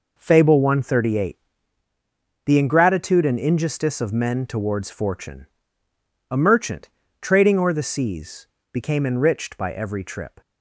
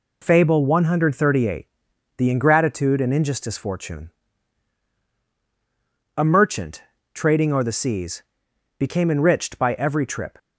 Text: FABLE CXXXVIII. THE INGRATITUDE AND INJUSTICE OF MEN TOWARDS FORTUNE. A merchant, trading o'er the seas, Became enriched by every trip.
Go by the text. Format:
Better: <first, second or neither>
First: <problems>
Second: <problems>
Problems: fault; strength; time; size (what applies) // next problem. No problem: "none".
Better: first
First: none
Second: skips "OF MEN TOWARDS"; at 3.5 s